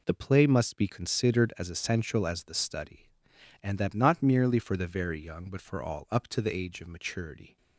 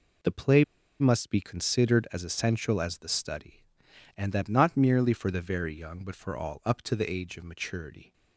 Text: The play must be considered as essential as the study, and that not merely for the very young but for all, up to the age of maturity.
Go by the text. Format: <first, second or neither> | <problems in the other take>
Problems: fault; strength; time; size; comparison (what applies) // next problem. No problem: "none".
first | pauses between "play" and "must"; at 0.6 s; 0.36 s long